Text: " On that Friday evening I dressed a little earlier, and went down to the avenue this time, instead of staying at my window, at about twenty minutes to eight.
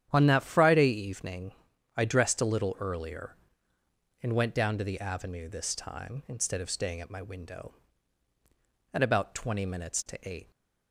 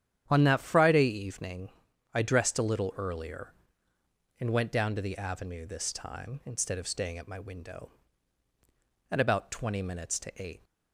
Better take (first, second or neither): neither